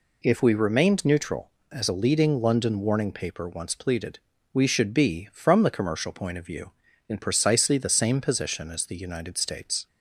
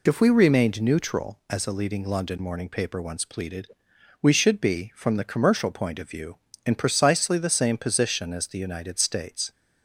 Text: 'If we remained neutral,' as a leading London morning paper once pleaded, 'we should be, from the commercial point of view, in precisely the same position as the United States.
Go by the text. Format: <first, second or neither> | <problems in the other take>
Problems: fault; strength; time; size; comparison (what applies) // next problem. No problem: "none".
second | says "warning" for "morning"; at 2.8 s